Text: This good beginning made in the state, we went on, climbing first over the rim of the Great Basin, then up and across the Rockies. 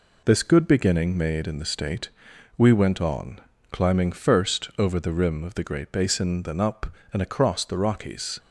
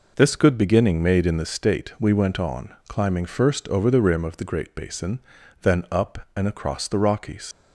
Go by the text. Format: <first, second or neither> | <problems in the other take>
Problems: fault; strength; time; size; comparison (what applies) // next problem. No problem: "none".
first | leaves "Rockies" unfinished; at 7.5 s; 70 ms